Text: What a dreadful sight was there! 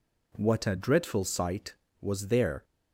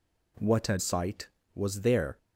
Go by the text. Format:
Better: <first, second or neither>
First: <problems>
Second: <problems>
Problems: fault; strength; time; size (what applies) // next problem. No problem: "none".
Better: first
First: none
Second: skips "dreadful"; at 0.7 s